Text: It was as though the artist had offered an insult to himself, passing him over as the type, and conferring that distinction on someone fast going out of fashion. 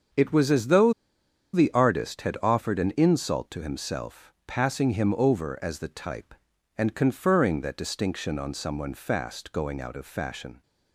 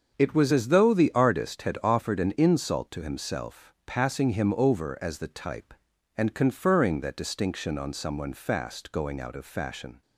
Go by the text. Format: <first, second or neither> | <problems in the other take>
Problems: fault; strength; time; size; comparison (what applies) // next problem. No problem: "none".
second | starts louder than the rest; until 1.8 s; 7 dB; also in the second // pauses between "though" and "the"; noticeable; at 0.9 s; 0.61 s long